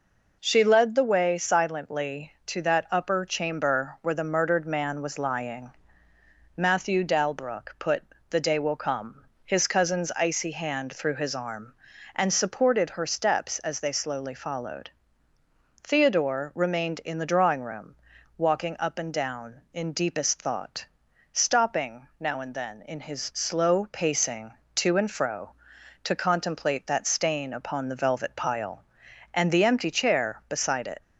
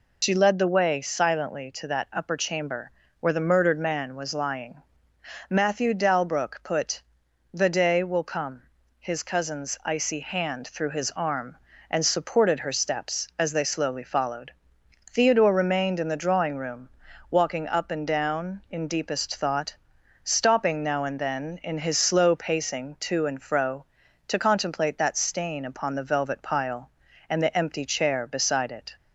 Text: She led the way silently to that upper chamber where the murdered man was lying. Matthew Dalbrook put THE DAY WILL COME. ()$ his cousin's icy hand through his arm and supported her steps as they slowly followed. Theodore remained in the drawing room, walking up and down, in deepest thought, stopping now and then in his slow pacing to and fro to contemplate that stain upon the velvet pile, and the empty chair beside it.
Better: first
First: pauses between "put" and "THE"; slight; at 8.0 s; 0.28 s long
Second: loses the start of "She"; at 0.2 s; 75 ms // pauses between "chamber" and "where"; slight; at 2.9 s; 0.30 s long // pauses between "put" and "THE"; noticeable; at 7.0 s; 0.50 s long

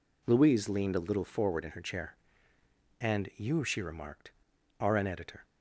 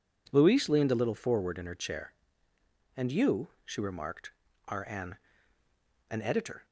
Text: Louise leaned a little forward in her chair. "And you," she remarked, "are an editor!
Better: first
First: none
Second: says "an" twice; at 6.1 s

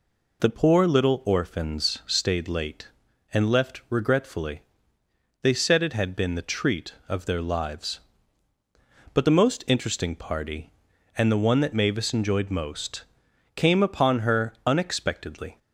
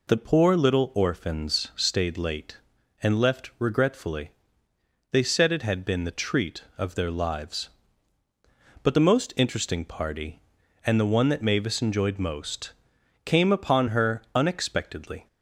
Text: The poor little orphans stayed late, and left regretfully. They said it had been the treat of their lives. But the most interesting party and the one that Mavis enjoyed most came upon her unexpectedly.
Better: neither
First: pauses between "most" and "came"; noticeable; at 13.0 s; 0.53 s long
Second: pauses between "most" and "came"; noticeable; at 12.7 s; 0.54 s long

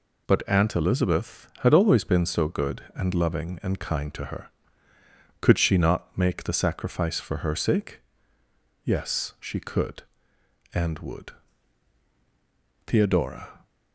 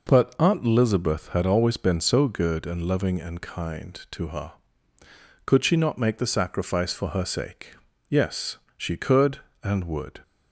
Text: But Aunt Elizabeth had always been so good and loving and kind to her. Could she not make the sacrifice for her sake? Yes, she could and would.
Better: second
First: goes on to say "Theodora"; noticeable; from 12.8 s on; 0.80 s long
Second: none

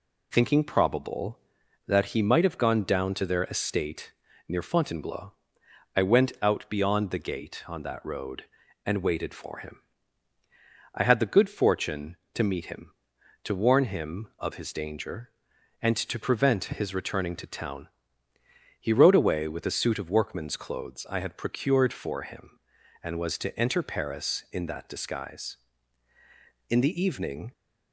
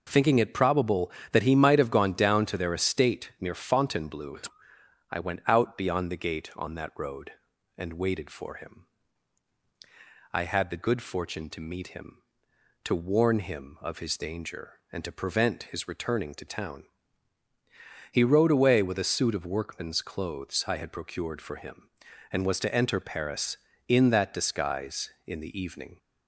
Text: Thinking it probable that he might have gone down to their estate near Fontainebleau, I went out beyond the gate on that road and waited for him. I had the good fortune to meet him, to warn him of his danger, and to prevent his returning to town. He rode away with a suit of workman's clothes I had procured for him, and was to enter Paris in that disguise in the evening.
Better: second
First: skips "it"; at 0.6 s // pauses between "estate" and "near"; slight; at 4.1 s; 0.36 s long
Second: none

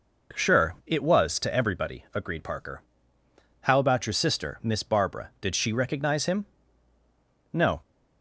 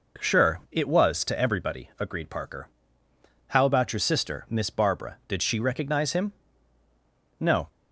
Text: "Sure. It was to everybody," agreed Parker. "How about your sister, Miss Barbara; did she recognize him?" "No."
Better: neither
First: none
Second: none

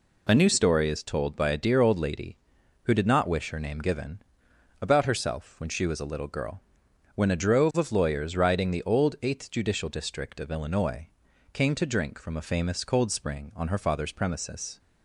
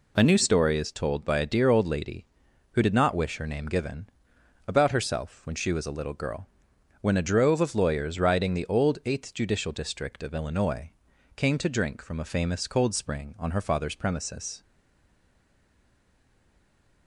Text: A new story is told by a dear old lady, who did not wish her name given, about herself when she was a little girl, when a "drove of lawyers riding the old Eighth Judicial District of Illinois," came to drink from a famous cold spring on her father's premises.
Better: first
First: none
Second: stays silent after the last word; from 14.6 s on; 2.4 s long

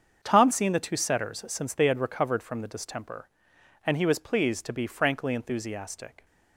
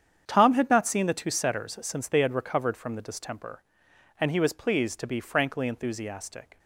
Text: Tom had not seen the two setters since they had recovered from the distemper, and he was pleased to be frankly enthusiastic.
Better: second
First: starts louder than the rest; strong; until 1.2 s; 7.5 dB // skips "had not"; at 0.5 s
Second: starts louder than the rest; strong; until 1.2 s; 8.5 dB

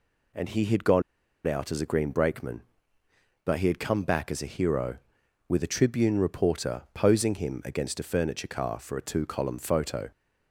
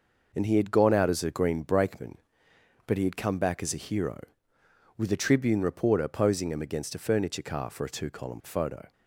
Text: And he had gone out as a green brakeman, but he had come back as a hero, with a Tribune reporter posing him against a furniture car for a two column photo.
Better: second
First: pauses between "gone" and "out"; at 1.0 s; 0.44 s long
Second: none

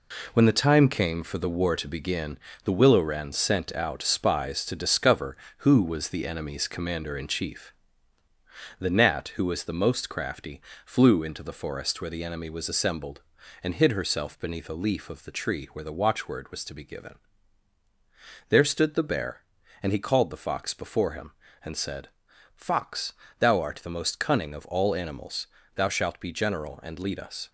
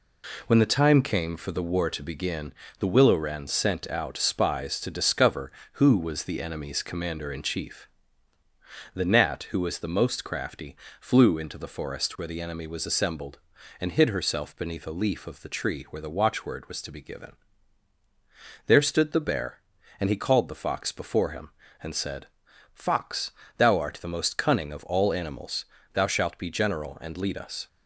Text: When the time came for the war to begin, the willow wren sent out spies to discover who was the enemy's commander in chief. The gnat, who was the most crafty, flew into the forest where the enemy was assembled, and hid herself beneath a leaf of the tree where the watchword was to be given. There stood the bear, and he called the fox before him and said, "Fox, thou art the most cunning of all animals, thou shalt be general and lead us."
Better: second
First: gets quieter; noticeable; throughout; 5.5 dB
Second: none

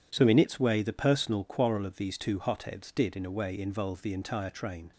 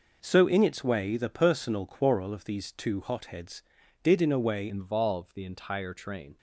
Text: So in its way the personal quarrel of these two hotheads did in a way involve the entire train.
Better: first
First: none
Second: changes voice at "involve"; from 4.6 s on; 1.7 s long

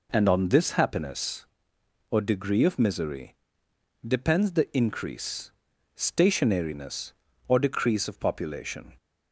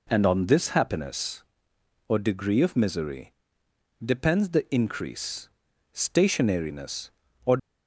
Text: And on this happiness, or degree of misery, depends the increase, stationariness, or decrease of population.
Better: first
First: none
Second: stops before "decrease of population"; at 7.5 s

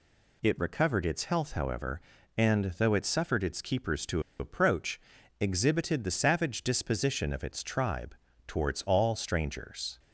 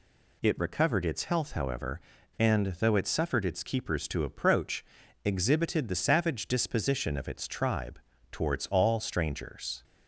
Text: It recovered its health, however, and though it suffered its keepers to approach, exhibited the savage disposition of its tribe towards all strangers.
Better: second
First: pauses between "to" and "approach"; slight; at 4.2 s; 0.18 s long // pauses between "tribe" and "towards"; slight; at 8.1 s; 0.32 s long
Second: pauses between "tribe" and "towards"; slight; at 7.9 s; 0.32 s long

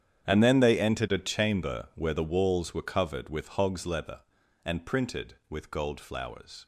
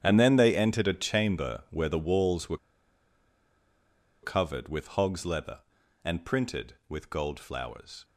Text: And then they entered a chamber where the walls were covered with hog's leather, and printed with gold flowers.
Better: first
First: starts louder than the rest; strong; until 1.2 s; 9 dB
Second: starts louder than the rest; strong; until 1.0 s; 9 dB // pauses between "were" and "covered"; strong; at 2.5 s; 1.6 s long

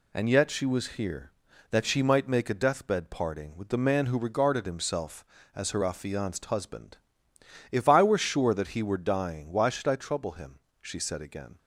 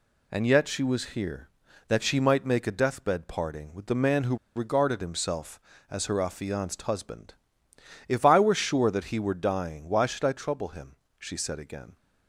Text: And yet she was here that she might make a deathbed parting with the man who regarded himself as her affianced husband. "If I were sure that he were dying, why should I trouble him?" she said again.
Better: first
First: none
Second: pauses between "who" and "regarded"; slight; at 4.3 s; 0.19 s long

